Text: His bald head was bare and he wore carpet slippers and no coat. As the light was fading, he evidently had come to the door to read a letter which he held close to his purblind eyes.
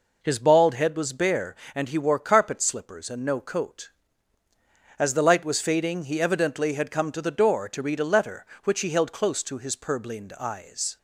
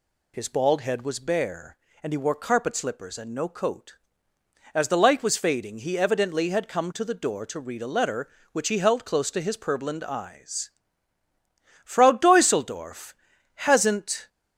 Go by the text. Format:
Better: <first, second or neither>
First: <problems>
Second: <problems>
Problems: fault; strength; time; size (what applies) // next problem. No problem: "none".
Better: first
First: none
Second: goes on to say "Frau Deuseldorf hasn't"; strong; from 11.8 s on; 2.4 s long